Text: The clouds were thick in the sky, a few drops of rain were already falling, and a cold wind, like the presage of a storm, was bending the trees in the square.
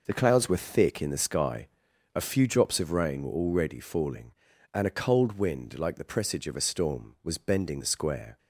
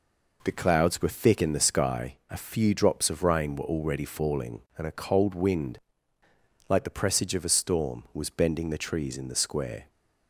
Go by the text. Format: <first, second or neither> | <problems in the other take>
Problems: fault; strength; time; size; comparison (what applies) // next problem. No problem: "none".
second | skips "the trees in"; at 7.8 s